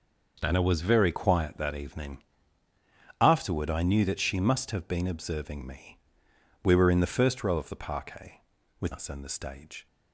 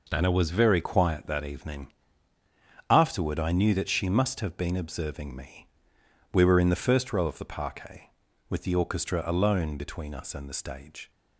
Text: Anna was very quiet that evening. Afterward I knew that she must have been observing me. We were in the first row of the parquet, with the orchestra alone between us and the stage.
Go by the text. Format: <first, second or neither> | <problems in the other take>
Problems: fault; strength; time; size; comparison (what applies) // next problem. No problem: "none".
second | skips "the orchestra alone between"; at 8.9 s